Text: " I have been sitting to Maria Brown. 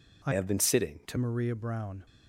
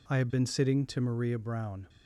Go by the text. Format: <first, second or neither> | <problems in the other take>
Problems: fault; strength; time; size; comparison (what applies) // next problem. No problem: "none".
second | changes voice from "have" to "to"; from 0.3 to 1.1 s; 0.8 s long